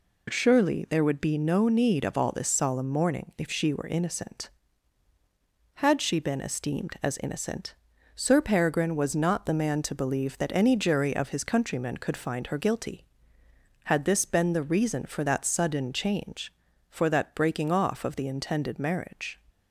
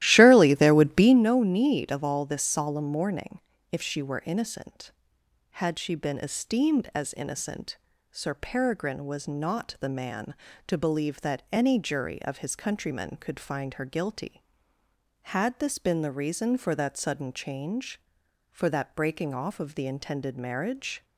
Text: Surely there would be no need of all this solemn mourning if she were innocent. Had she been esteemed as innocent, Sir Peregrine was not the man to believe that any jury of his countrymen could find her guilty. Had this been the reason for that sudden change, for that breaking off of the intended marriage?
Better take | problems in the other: first | starts louder than the rest; strong; until 1.3 s; 15 dB // pauses between "mourning" and "if"; slight; at 3.3 s; 0.32 s long

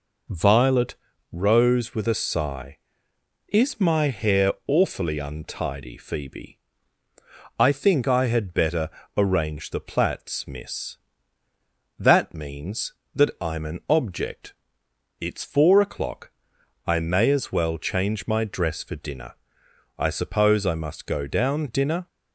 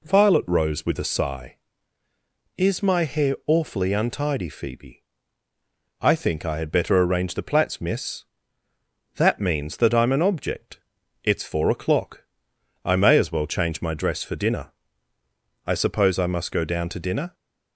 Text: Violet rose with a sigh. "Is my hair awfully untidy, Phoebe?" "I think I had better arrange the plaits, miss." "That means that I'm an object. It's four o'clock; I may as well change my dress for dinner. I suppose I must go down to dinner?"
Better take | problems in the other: second | pauses between "Violet" and "rose"; slight; at 0.9 s; 0.36 s long // pauses between "better" and "arrange"; slight; at 8.8 s; 0.26 s long // skips "to"; at 21.6 s

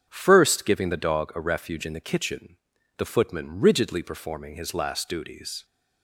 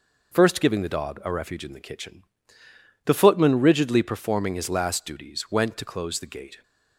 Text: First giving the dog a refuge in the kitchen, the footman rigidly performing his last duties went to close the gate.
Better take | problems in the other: second | starts louder than the rest; strong; until 1.0 s; 7.5 dB // stops before "went to close the gate"; at 5.6 s

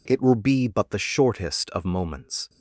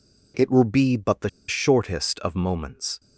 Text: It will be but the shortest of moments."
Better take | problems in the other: first | pauses between "the" and "shortest"; slight; at 1.2 s; 0.19 s long

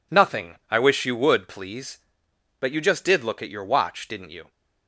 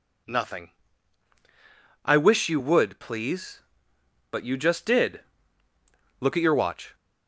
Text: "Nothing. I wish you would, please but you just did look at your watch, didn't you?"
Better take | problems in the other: first | pauses between "did" and "look"; at 5.2 s; 1.0 s long // stops before "didn't you"; at 6.9 s

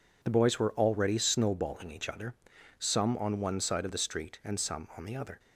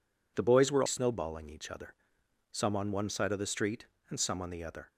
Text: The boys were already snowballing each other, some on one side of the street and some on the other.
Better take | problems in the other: first | skips "already"; at 0.8 s

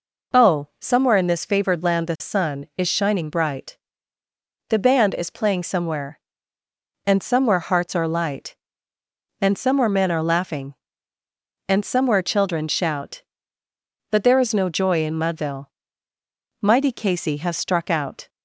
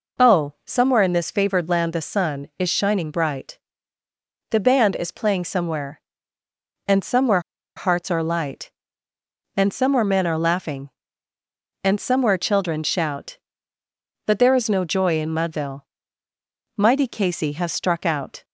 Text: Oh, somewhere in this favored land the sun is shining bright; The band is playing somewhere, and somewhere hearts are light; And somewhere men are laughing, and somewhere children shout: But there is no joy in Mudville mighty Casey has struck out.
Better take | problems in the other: first | pauses between "somewhere" and "hearts"; at 7.3 s; 0.36 s long // pauses between "Mudville" and "mighty"; noticeable; at 15.8 s; 0.94 s long; noticeable in the first

